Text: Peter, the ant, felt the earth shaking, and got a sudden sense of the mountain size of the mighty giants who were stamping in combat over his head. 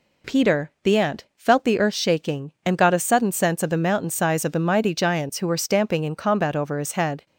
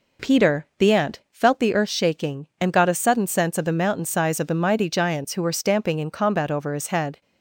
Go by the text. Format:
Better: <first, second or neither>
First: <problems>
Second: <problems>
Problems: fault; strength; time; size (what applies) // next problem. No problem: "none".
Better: first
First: none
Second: starts louder than the rest; until 1.4 s; 3.5 dB